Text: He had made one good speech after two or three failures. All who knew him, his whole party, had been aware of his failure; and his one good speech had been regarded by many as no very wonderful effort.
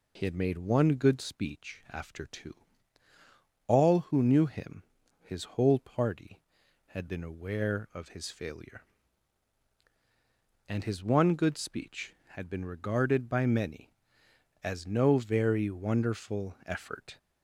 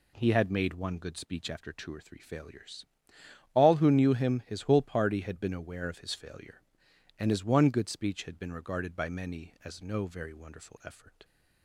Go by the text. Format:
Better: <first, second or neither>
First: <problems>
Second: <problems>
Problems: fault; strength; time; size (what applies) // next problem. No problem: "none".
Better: second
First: skips "or three failures"; at 3.1 s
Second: none